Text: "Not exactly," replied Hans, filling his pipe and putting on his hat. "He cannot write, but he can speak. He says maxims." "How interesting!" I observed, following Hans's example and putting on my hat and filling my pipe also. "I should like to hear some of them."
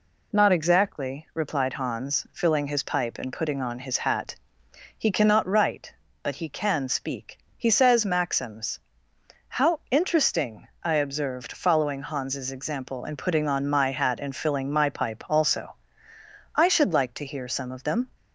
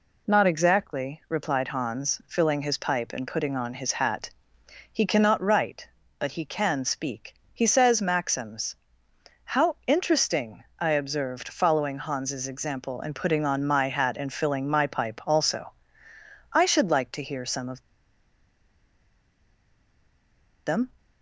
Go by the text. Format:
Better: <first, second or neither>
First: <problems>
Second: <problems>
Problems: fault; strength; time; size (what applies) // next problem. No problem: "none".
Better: first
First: none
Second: pauses between "of" and "them"; strong; at 17.8 s; 2.8 s long